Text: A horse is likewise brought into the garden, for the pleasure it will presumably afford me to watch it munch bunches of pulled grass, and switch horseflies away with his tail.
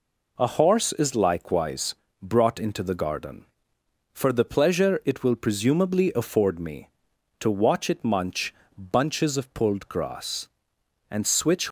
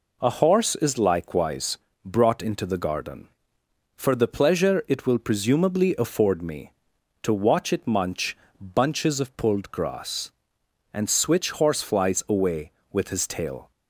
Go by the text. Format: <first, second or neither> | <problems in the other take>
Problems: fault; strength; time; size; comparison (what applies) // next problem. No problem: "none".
second | pauses between "likewise" and "brought"; slight; at 1.9 s; 0.28 s long; slight in the second // pauses between "munch" and "bunches"; slight; at 8.5 s; 0.22 s long; slight in the second // stops before "horseflies away with his tail"; at 11.6 s